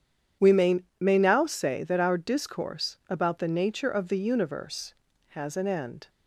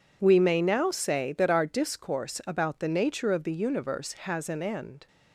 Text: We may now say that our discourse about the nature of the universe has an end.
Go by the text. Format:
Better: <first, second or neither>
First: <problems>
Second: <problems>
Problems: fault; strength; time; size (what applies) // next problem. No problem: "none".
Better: second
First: starts louder than the rest; strong; until 1.5 s; 9 dB // says "may" twice; at 0.9 s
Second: none